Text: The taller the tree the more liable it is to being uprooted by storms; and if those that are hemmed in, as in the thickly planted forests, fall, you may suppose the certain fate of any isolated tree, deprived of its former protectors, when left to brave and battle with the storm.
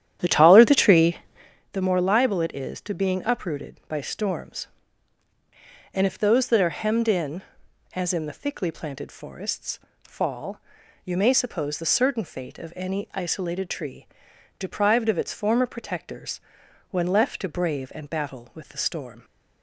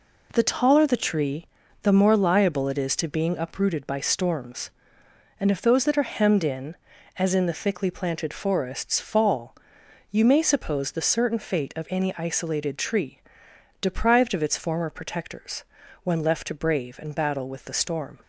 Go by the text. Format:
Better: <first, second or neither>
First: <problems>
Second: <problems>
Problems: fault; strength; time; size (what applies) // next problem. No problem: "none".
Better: second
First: starts louder than the rest; strong; until 1.6 s; 10.5 dB // pauses between "tree" and "the"; noticeable; at 1.1 s; 0.56 s long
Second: pauses between "tree" and "the"; slight; at 1.4 s; 0.36 s long